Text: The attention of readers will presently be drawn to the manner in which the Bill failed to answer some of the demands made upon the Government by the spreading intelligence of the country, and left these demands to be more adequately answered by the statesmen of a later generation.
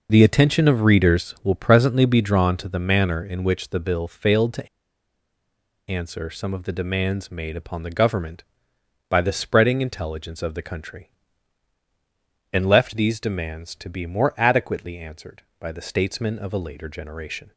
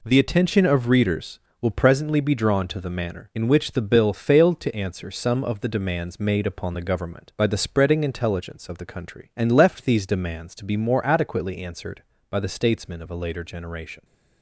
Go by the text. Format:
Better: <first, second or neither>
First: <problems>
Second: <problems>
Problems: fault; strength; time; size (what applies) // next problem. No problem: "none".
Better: second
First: pauses between "to" and "answer"; at 4.6 s; 1.2 s long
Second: none